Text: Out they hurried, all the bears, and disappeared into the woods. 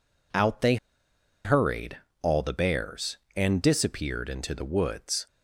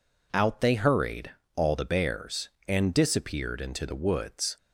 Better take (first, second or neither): second